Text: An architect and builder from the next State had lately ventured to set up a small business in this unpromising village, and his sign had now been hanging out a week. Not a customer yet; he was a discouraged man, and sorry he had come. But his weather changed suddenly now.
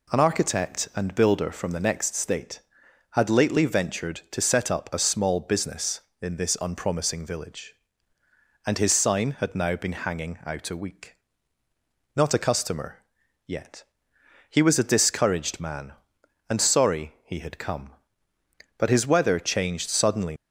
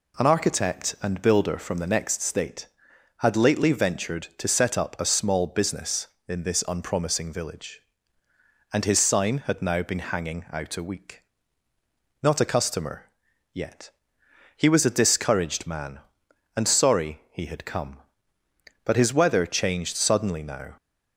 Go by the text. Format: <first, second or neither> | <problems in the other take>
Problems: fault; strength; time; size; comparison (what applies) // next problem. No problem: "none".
second | pauses between "customer" and "yet"; noticeable; at 13.0 s; 0.46 s long; noticeable in the second // stops before "now"; at 20.3 s